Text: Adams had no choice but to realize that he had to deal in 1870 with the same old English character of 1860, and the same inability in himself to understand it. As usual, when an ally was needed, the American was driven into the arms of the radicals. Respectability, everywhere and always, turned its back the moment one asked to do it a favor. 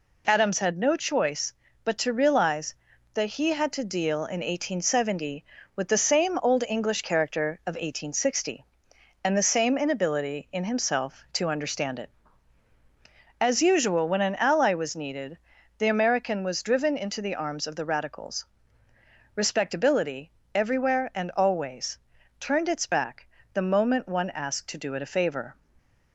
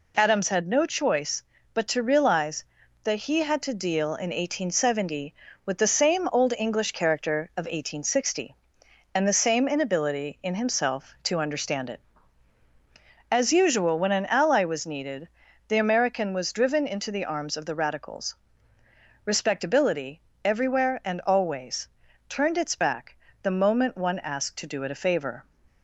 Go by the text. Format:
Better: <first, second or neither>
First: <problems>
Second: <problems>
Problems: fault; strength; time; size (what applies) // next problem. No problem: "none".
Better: neither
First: pauses between "back" and "the"; slight; at 23.2 s; 0.26 s long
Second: pauses between "back" and "the"; slight; at 23.1 s; 0.26 s long